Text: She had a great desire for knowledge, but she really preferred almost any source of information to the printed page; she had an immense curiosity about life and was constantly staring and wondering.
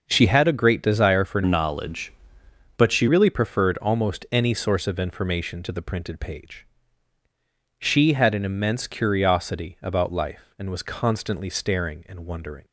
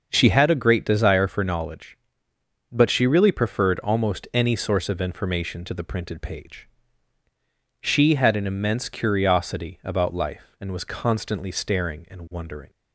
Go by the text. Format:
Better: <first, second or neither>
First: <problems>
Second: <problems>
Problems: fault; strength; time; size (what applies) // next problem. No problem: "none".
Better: second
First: starts louder than the rest; noticeable; until 1.0 s; 6 dB // changes voice from "knowledge" to "she"; from 1.4 to 3.0 s; 1.6 s long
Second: starts louder than the rest; noticeable; until 1.1 s; 6 dB